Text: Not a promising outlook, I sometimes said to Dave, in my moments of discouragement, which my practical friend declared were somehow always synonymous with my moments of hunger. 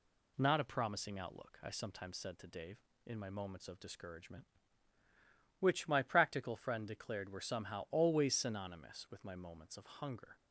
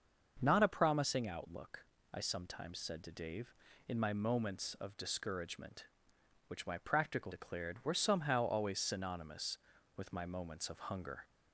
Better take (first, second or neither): first